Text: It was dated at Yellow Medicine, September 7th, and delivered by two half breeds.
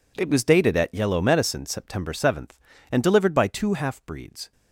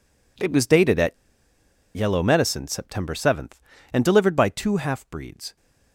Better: first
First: none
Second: pauses between "at" and "Yellow"; noticeable; at 1.1 s; 0.80 s long

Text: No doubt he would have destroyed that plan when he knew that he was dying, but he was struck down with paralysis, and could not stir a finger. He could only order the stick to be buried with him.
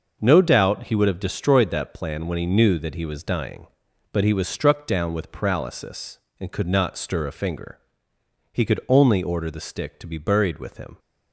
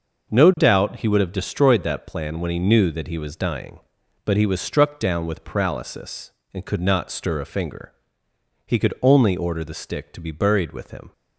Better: neither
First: none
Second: none

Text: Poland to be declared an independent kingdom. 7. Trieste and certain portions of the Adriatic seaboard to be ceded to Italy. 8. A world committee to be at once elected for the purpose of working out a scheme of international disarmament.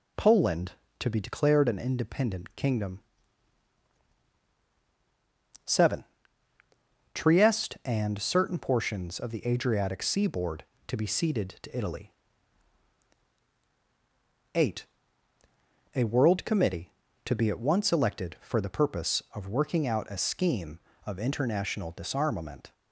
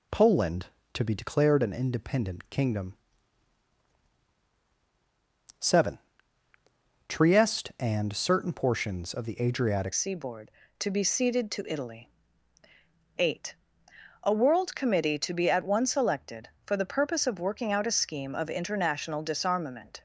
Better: first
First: none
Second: changes voice at "seaboard"; from 9.9 s on; 10.1 s long

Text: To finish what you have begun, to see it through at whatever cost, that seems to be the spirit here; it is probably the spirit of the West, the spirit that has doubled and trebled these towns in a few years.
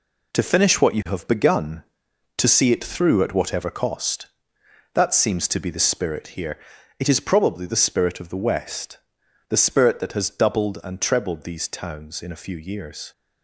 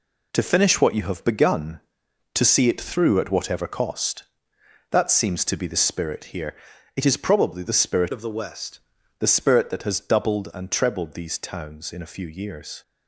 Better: first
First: none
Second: changes voice from "of" to "West"; from 8.1 to 8.7 s; 0.6 s long

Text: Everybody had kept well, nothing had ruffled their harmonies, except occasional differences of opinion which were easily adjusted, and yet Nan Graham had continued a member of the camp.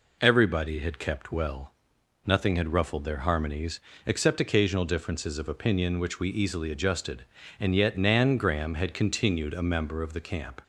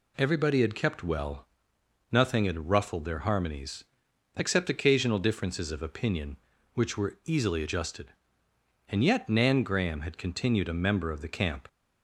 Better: second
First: says "we" for "were"; at 6.1 s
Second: none

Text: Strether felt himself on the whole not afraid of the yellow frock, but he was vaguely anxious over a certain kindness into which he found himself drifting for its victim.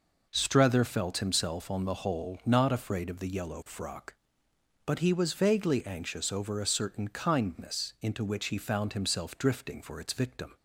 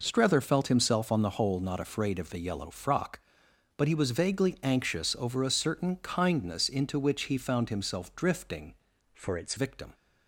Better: first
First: none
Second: changes voice from "for" to "its"; from 9.1 to 9.5 s; 0.4 s long

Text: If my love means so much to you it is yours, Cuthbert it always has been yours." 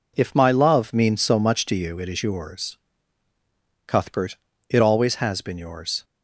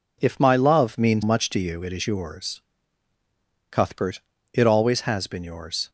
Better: first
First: pauses between "Cuthbert" and "it"; slight; at 4.3 s; 0.34 s long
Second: skips "so"; at 1.2 s // pauses between "Cuthbert" and "it"; slight; at 4.1 s; 0.34 s long

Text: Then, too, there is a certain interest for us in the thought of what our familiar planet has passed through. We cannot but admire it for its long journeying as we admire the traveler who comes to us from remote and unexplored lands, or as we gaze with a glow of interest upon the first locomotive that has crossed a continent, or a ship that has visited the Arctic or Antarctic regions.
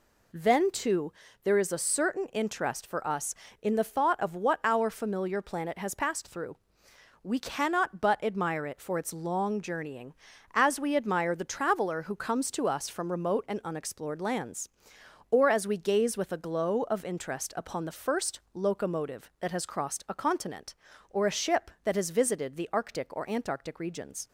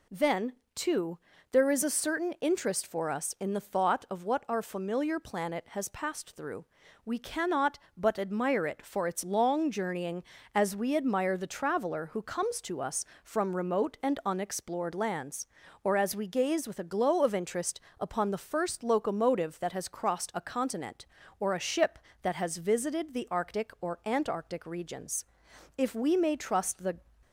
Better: first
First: none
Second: pauses between "interest" and "upon"; slight; at 17.7 s; 0.20 s long // goes on to say "If we may trust the"; noticeable; from 25.7 s on; 1.1 s long

